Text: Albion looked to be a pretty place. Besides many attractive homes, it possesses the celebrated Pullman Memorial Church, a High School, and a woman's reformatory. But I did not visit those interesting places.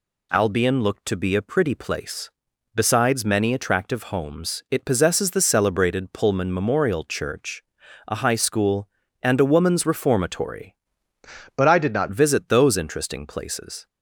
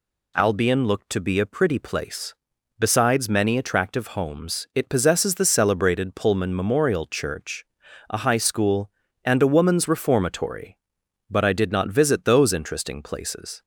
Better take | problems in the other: second | changes voice from "But" to "not"; from 11.5 to 12.0 s; 0.5 s long

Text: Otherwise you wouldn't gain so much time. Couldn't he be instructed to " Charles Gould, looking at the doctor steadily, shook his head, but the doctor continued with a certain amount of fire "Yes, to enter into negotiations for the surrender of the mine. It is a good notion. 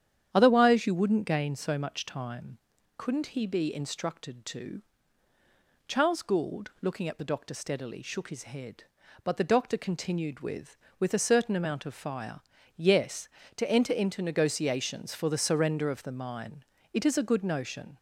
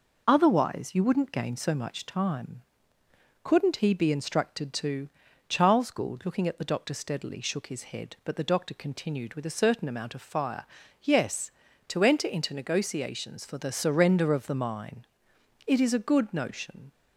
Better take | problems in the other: second | starts louder than the rest; strong; until 1.3 s; 9.5 dB // says "with" twice; at 10.9 s // pauses between "fire" and "Yes"; at 12.3 s; 0.38 s long; also in the second

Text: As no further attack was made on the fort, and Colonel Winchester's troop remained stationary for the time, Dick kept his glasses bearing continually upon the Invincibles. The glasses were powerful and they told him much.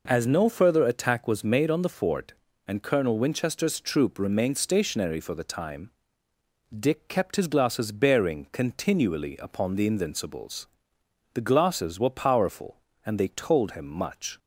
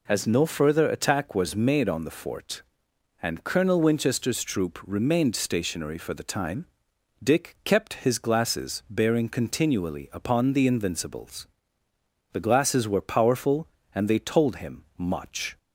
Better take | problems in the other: neither | none

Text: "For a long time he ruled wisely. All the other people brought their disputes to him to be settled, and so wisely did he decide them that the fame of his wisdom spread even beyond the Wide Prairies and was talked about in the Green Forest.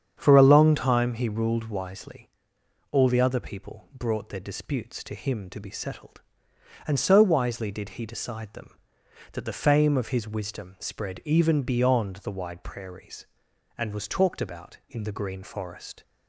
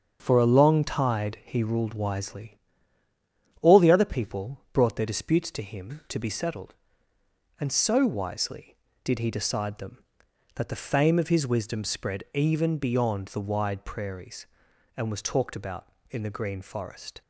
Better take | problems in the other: first | starts louder than the rest; strong; until 1.2 s; 7 dB; strong in the first // says "tide" for "time"; at 0.8 s

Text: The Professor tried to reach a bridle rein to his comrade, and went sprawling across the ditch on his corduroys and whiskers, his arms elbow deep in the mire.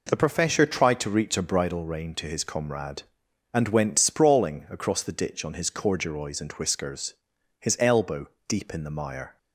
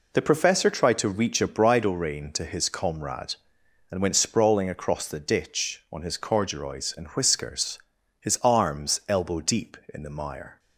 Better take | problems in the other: second | skips "arms"; at 7.7 s // pauses between "elbow" and "deep"; slight; at 8.2 s; 0.20 s long

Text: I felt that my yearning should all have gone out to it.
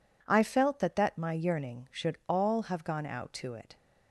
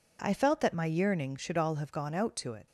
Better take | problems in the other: second | says "that" twice; at 0.9 s

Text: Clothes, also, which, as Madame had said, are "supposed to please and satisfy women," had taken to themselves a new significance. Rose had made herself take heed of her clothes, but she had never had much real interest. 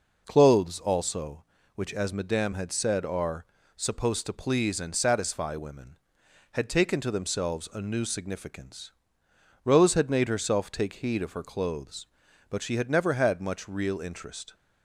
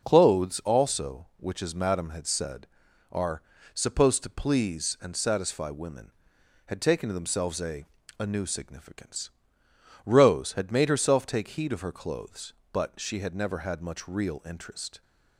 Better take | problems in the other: first | pauses between "are" and "supposed"; slight; at 3.4 s; 0.32 s long; slight in the first // says "a" twice; at 8.1 s

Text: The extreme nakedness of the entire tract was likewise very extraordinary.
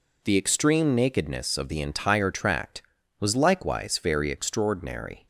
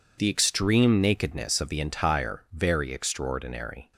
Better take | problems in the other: first | skips "tract was likewise"; at 2.4 s

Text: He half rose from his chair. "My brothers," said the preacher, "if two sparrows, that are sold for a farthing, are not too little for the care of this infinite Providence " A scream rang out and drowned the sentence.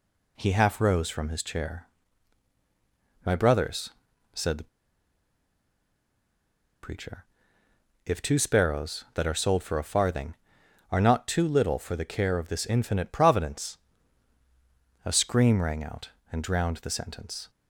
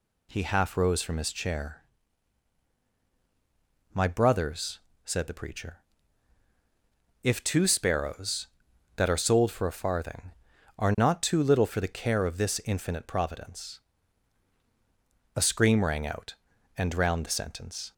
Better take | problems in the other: second | pauses between "the" and "preacher"; strong; at 4.6 s; 2.1 s long

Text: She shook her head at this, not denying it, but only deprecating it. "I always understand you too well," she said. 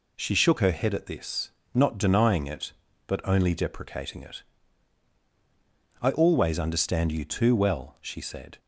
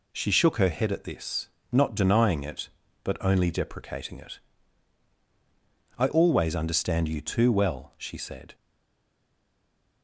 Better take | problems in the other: first | stays silent after the last word; noticeable; from 8.5 s on; 1.5 s long

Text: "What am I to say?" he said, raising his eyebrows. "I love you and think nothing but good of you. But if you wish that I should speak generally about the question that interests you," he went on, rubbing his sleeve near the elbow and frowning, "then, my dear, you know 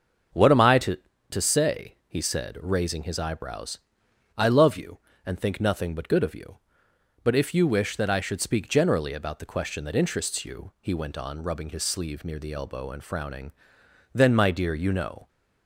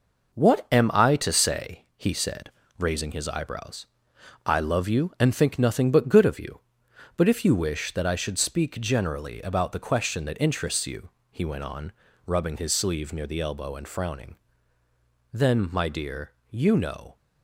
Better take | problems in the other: second | starts louder than the rest; until 1.6 s; 7 dB // says "to" twice; at 1.2 s

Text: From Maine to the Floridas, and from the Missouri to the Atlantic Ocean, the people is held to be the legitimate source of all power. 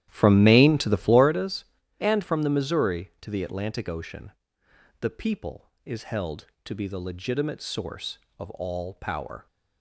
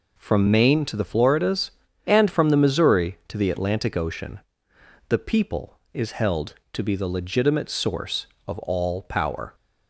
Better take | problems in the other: second | starts louder than the rest; strong; until 1.4 s; 12 dB

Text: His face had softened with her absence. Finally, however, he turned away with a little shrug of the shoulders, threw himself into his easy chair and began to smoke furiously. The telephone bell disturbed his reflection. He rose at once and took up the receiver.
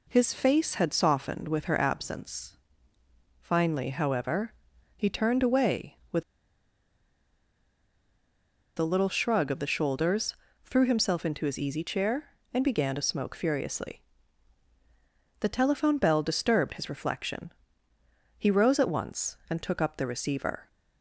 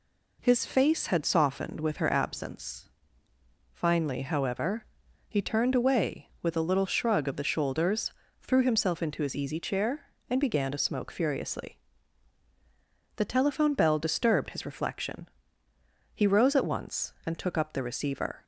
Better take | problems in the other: second | pauses between "with" and "a"; strong; at 6.2 s; 2.5 s long

